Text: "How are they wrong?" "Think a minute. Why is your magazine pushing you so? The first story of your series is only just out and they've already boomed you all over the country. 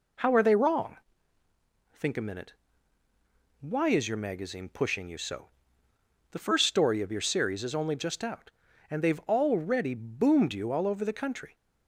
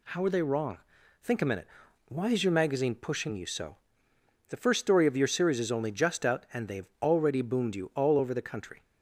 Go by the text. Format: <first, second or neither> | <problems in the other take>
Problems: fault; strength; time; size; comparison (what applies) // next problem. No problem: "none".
neither | none